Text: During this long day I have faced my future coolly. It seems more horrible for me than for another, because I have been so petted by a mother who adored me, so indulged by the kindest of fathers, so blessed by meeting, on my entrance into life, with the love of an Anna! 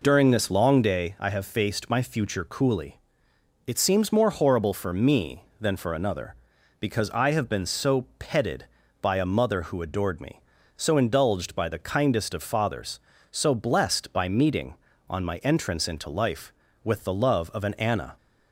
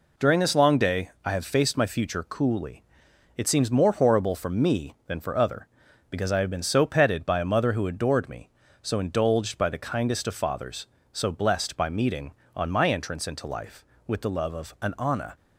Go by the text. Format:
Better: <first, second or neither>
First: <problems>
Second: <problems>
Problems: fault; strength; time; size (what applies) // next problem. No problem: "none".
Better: first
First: none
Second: pauses between "day" and "I"; slight; at 1.0 s; 0.16 s long // says "other" for "another"; at 5.3 s